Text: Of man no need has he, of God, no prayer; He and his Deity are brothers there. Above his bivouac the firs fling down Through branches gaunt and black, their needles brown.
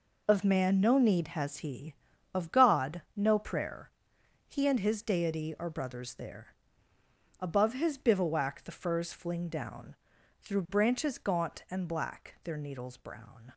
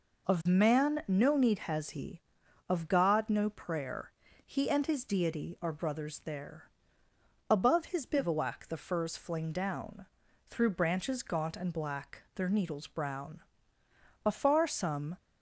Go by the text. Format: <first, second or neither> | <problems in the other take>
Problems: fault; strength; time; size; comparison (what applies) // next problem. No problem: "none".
first | pauses between "down" and "Through"; noticeable; at 10.0 s; 0.46 s long; also in the first // goes on to say "Afar some"; noticeable; from 14.2 s on; 0.94 s long